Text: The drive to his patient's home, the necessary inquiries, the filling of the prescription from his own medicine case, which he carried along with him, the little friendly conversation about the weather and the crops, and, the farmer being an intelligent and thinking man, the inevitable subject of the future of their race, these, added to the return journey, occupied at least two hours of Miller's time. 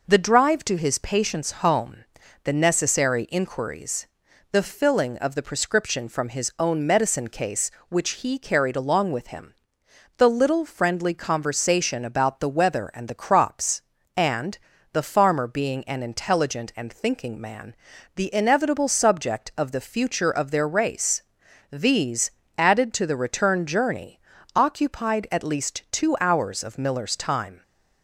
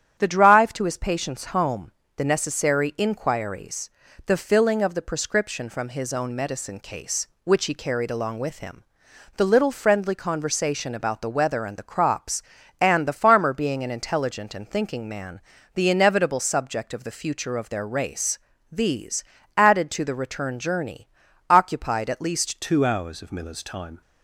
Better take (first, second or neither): first